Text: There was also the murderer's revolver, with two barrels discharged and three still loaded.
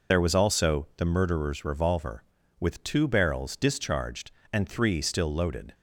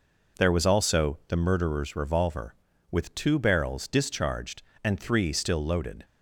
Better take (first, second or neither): second